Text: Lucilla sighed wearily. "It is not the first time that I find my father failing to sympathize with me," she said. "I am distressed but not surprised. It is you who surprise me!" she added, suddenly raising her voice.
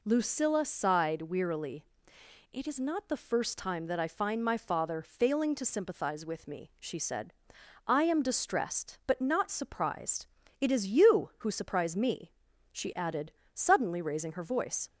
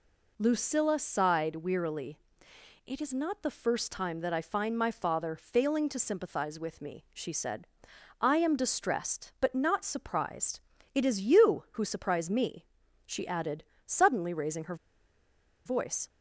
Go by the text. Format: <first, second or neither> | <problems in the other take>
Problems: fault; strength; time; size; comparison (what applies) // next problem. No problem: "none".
first | pauses between "her" and "voice"; noticeable; at 14.7 s; 0.90 s long